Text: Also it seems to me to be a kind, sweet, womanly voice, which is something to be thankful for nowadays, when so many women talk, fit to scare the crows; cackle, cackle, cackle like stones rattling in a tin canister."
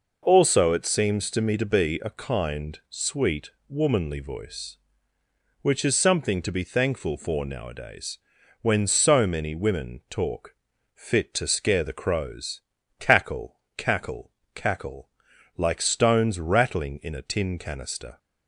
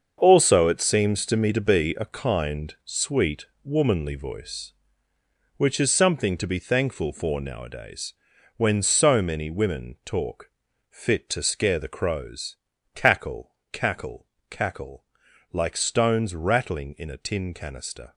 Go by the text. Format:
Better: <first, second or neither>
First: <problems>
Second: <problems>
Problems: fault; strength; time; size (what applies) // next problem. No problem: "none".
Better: first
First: pauses between "cackle" and "like"; noticeable; at 15.0 s; 0.48 s long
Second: gets quieter; strong; throughout; 10.5 dB // pauses between "cackle" and "like"; noticeable; at 15.0 s; 0.48 s long